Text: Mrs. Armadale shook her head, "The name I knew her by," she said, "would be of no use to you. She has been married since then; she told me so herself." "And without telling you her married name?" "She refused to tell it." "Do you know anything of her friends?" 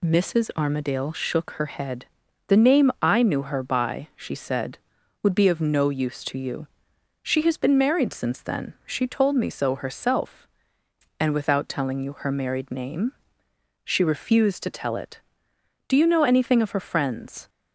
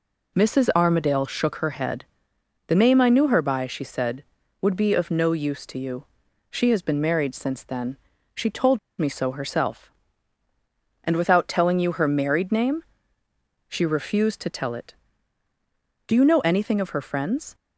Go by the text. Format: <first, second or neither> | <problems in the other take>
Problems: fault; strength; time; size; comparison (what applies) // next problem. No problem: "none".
first | pauses between "told" and "me"; slight; at 8.7 s; 0.19 s long